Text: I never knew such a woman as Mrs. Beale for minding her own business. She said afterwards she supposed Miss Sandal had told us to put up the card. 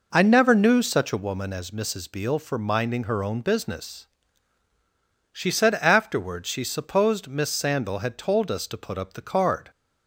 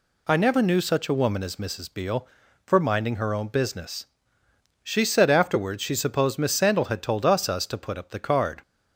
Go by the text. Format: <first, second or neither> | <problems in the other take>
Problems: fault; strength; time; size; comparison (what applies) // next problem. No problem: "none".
first | says "us" twice; at 7.4 s